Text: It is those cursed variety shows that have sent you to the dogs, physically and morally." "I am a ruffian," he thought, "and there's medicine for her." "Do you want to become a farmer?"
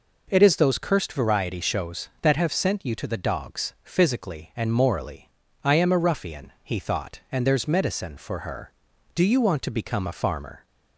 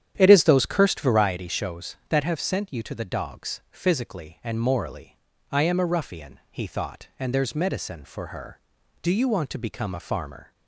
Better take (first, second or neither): first